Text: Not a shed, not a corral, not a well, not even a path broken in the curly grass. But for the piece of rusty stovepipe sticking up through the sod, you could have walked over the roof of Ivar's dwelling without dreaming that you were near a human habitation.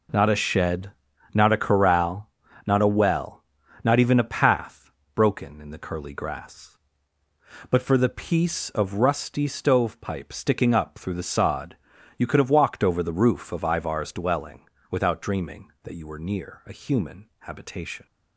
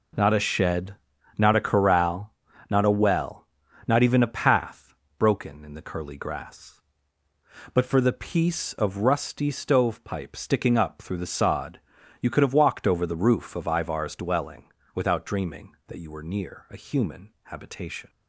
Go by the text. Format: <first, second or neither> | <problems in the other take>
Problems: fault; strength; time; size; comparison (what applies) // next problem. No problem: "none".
neither | pauses between "path" and "broken"; slight; the same in both // pauses between "dwelling" and "without"; slight; the same in both